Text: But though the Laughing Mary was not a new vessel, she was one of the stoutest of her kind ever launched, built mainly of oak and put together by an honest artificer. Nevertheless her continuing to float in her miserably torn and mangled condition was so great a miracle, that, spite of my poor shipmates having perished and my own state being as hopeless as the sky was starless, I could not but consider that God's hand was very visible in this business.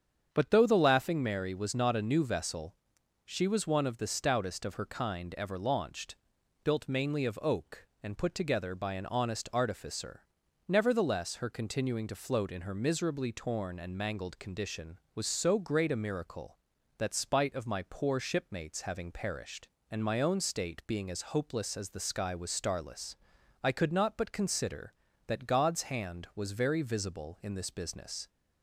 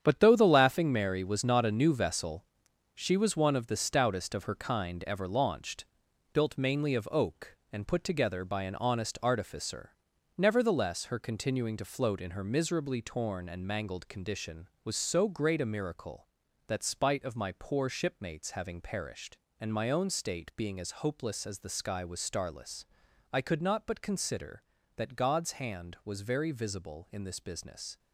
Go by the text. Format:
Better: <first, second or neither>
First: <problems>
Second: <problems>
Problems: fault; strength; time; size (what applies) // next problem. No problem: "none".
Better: first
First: starts louder than the rest; strong; until 1.3 s; 8 dB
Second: gets quieter; strong; throughout; 9.5 dB // starts louder than the rest; strong; until 1.0 s; 8.5 dB